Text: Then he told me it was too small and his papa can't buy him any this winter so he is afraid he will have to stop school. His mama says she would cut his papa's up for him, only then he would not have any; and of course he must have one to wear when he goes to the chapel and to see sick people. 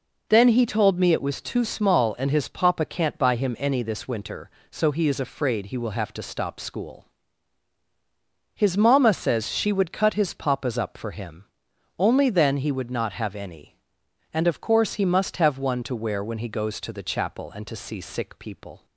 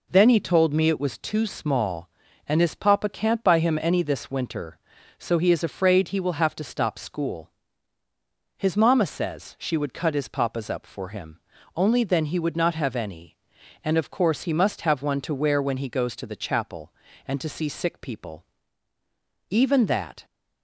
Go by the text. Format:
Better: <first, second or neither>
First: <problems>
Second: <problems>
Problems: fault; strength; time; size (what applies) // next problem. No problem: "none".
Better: first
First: none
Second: goes on to say "Even that"; noticeable; from 19.4 s on; 0.76 s long